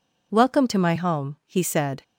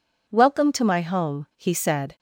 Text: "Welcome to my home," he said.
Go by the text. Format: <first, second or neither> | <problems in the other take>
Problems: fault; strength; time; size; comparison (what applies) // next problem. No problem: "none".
neither | none